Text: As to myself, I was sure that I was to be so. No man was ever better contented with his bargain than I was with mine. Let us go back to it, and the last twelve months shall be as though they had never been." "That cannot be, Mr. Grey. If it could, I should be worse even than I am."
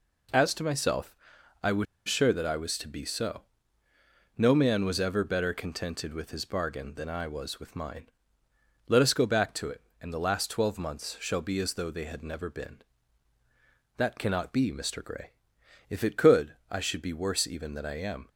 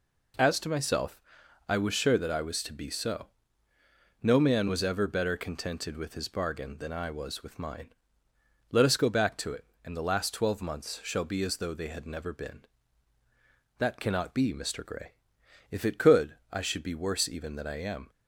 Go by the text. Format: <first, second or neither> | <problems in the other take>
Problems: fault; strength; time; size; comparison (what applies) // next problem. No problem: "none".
second | pauses between "was" and "sure"; slight; at 1.8 s; 0.22 s long